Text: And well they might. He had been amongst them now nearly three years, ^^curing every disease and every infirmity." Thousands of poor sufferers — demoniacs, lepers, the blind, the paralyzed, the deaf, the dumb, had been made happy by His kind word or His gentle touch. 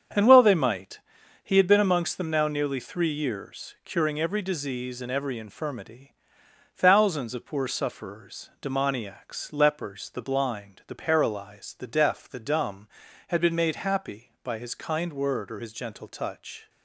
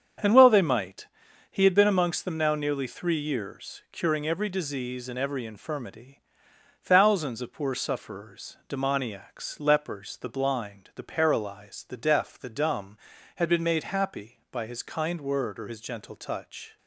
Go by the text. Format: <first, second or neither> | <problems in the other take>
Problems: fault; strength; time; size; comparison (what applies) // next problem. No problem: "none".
neither | starts louder than the rest; strong; the same in both